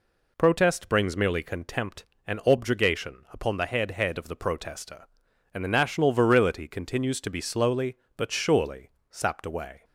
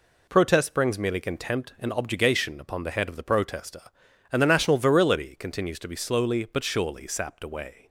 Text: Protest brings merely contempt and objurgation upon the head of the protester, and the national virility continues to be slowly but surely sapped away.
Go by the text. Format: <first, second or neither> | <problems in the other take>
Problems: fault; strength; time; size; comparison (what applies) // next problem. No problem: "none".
second | says "head" twice; at 3.9 s // pauses between "surely" and "sapped"; slight; at 8.8 s; 0.20 s long